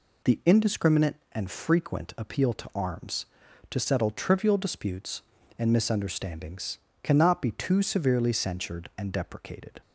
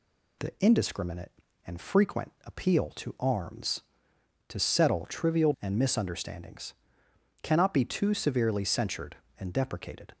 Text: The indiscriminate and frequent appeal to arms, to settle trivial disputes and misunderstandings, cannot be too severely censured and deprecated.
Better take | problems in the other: first | skips "disputes"; at 5.5 s

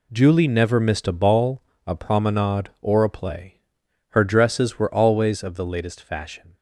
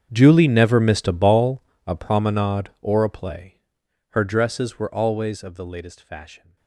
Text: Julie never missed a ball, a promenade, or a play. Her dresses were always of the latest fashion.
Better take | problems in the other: first | gets quieter; strong; throughout; 21.5 dB

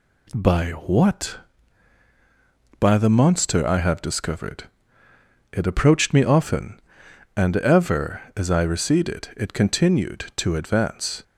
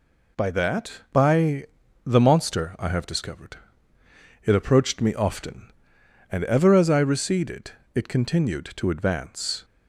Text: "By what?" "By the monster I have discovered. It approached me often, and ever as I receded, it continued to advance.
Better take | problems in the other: first | says "that" for "what"; at 0.5 s // pauses between "By" and "the"; at 1.6 s; 0.38 s long

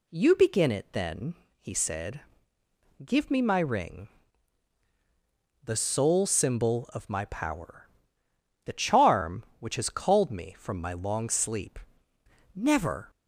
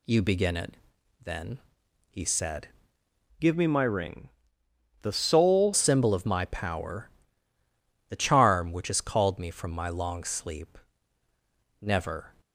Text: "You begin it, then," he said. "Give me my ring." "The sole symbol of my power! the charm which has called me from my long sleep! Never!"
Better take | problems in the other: first | changes voice from "Give" to "sole"; from 3.3 to 5.7 s; 2.4 s long

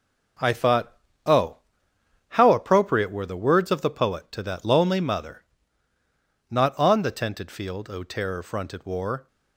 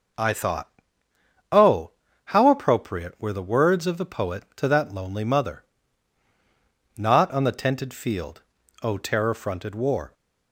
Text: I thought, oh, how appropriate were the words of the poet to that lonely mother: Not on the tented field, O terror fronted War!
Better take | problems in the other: second | gets quieter; strong; throughout; 8 dB

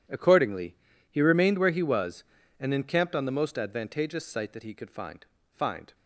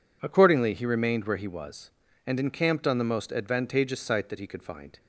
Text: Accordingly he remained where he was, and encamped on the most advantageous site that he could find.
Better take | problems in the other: second | pauses between "Accordingly" and "he"; slight; at 0.7 s; 0.34 s long // says "find" twice; at 5.5 s

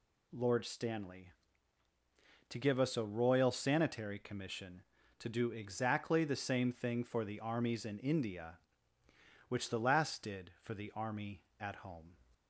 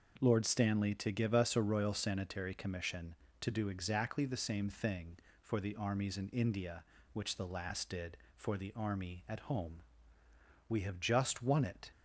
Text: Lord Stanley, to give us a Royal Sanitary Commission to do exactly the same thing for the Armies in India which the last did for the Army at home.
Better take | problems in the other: first | goes on to say "We have just won it"; noticeable; from 10.6 s on; 1.2 s long

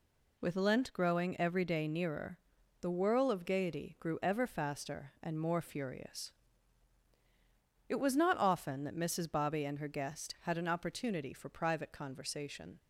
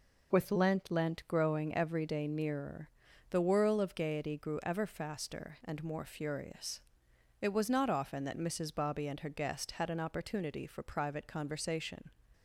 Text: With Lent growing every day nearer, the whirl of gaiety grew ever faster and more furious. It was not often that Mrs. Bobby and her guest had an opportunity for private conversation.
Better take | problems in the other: first | says "Lent" twice; at 0.8 s

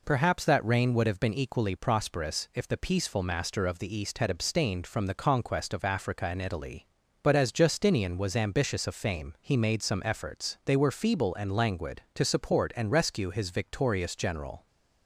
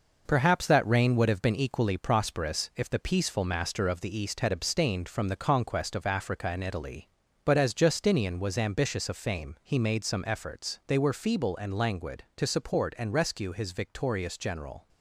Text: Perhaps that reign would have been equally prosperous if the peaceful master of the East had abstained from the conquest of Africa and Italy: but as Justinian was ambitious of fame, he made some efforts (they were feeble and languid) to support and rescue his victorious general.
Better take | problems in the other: first | gets quieter; noticeable; throughout; 6 dB

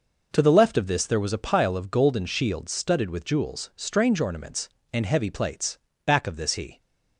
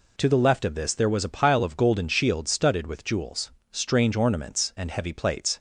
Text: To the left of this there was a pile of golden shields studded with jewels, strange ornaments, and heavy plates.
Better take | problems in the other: second | goes on to say "Back of this he"; noticeable; from 6.0 s on; 0.72 s long

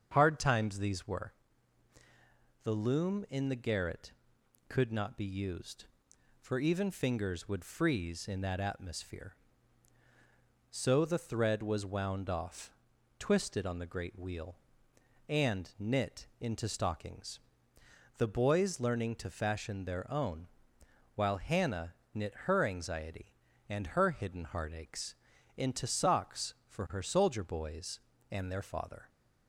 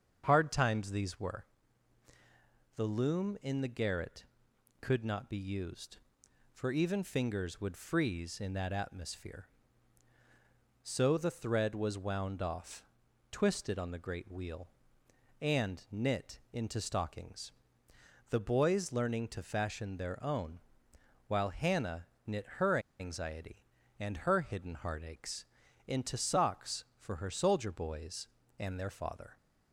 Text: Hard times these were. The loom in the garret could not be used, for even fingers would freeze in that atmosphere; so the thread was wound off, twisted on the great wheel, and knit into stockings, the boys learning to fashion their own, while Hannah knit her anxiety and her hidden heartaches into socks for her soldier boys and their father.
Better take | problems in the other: first | starts louder than the rest; strong; until 1.2 s; 7 dB; strong in the first // pauses between "knit" and "into"; slight; at 16.3 s; 0.16 s long; slight in the first // pauses between "Hannah" and "knit"; slight; at 22.0 s; 0.18 s long; slight in the first // pauses between "her" and "anxiety"; slight; at 22.7 s; 0.20 s long // pauses between "heartaches" and "into"; at 25.4 s; 0.42 s long; also in the first

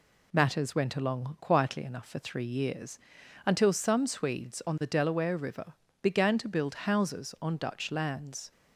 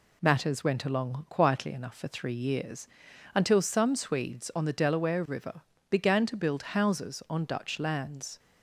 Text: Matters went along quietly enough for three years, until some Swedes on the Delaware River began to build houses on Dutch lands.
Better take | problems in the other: neither | pauses between "River" and "began"; slight; the same in both

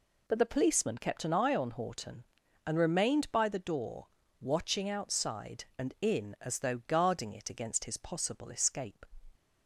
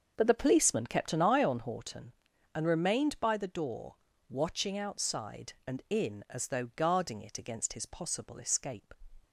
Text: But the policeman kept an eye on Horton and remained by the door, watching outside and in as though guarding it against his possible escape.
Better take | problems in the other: first | starts louder than the rest; until 1.8 s; 6.5 dB

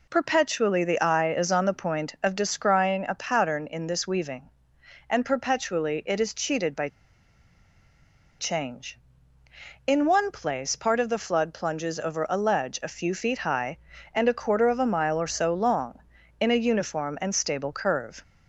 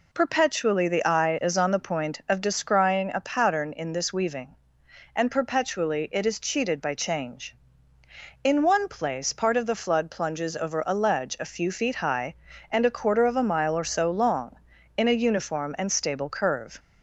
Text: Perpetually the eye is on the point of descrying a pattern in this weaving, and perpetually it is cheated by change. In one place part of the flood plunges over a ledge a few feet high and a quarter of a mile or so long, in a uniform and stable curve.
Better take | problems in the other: second | pauses between "by" and "change"; strong; at 6.8 s; 1.5 s long

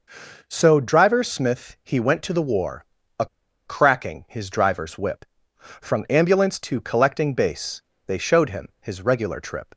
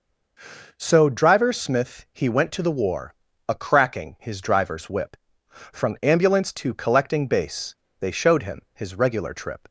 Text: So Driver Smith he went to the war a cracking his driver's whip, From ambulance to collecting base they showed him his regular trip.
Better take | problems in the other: second | pauses between "war" and "a"; slight; at 2.8 s; 0.34 s long; slight in the second // pauses between "a" and "cracking"; at 3.2 s; 0.41 s long // pauses between "base" and "they"; slight; at 7.8 s; 0.24 s long; slight in the second

